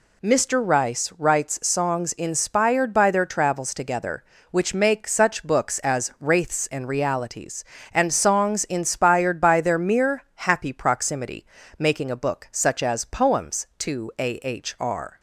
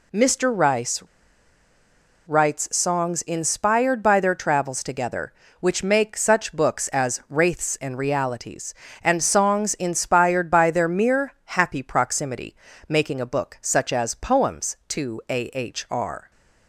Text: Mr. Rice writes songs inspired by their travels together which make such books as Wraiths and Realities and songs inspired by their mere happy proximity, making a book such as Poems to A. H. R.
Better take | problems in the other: first | pauses between "Rice" and "writes"; strong; at 1.0 s; 1.2 s long

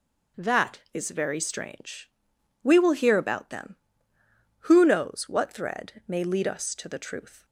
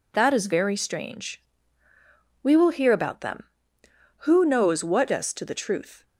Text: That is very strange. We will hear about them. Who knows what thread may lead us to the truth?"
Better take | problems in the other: first | skips "thread may lead"; at 5.1 s

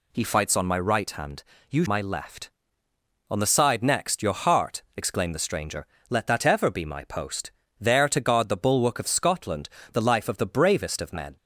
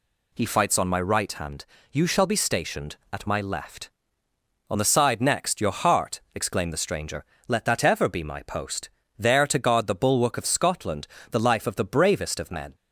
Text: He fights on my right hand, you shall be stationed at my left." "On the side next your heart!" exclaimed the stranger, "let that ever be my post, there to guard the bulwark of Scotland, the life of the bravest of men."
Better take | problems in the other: second | skips "shall be stationed at"; at 1.8 s

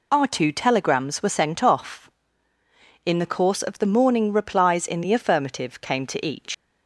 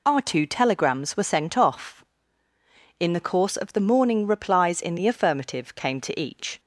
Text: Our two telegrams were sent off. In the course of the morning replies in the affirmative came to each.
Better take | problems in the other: second | leaves "each" unfinished; at 6.5 s; 110 ms

